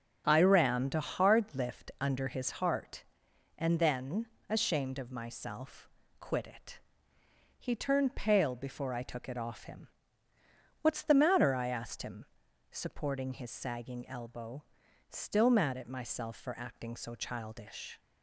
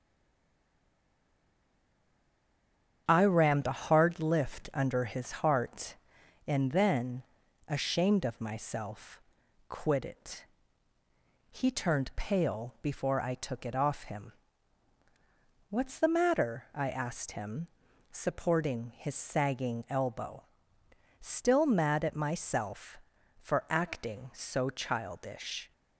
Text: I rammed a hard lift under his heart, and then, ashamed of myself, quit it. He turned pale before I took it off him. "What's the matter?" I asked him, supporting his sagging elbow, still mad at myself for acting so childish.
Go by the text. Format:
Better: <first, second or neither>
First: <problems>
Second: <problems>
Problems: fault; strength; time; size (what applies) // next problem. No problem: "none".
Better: first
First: starts louder than the rest; strong; until 1.2 s; 7 dB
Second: stays silent before the first word; strong; until 3.0 s; 3.0 s long // starts louder than the rest; strong; until 4.0 s; 8.5 dB